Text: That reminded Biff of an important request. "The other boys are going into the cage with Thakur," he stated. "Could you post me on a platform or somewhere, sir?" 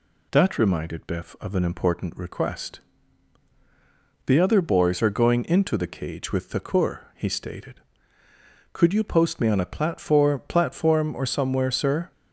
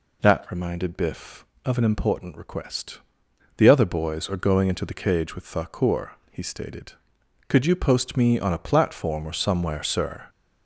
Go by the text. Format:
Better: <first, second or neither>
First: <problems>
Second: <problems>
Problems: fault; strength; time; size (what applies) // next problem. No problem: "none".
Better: second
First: says "platform" twice; at 10.4 s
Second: none